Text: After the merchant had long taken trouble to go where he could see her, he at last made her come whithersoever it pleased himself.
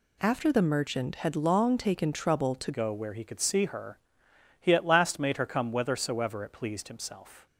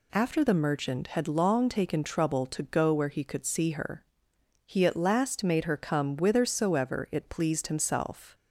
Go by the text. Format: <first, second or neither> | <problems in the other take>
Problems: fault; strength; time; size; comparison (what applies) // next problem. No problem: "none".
second | changes voice at "go"; from 2.7 s on; 4.7 s long